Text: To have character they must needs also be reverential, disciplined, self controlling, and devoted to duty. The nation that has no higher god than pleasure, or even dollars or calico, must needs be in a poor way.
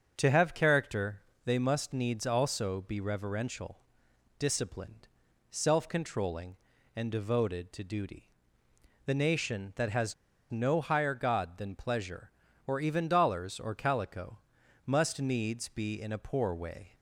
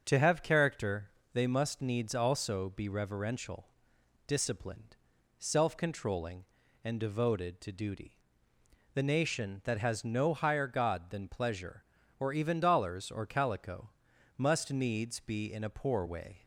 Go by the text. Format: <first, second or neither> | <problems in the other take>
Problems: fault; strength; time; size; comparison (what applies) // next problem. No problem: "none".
second | starts louder than the rest; until 1.1 s; 6.5 dB; also in the second // pauses between "character" and "they"; slight; at 1.2 s; 0.22 s long; slight in the second // pauses between "has" and "no"; at 10.1 s; 0.37 s long